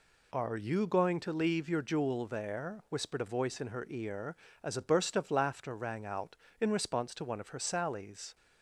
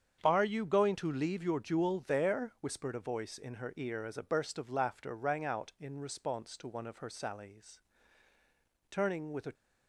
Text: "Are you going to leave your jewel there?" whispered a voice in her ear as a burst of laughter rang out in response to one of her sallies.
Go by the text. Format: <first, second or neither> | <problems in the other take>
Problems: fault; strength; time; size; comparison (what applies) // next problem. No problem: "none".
first | starts louder than the rest; strong; until 1.2 s; 8 dB // goes on to say "Turning with a"; noticeable; from 8.8 s on; 0.64 s long